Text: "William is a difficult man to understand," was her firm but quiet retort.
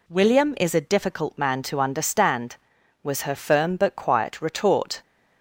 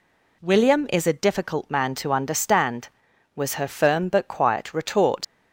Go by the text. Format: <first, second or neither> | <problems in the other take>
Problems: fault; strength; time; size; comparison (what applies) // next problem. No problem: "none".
first | leaves "retort" unfinished; at 5.2 s; 95 ms